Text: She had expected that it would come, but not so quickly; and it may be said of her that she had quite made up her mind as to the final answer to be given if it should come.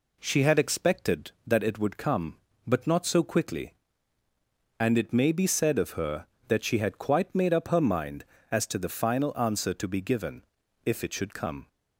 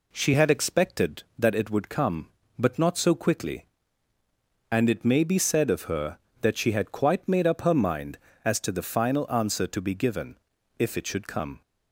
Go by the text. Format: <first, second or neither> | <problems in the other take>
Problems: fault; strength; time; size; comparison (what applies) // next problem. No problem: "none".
neither | pauses between "given" and "if"; the same in both